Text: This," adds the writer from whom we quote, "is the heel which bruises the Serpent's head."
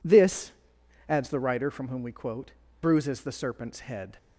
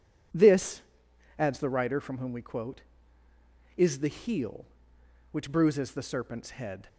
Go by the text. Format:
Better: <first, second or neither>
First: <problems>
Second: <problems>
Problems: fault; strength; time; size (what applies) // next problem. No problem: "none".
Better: second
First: skips "is the heel which"; at 2.6 s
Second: none